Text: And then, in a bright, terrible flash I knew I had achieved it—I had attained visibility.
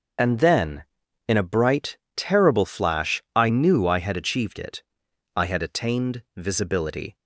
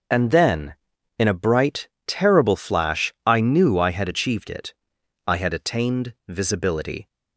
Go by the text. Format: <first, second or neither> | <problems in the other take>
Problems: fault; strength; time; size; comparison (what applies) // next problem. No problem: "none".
neither | starts louder than the rest; the same in both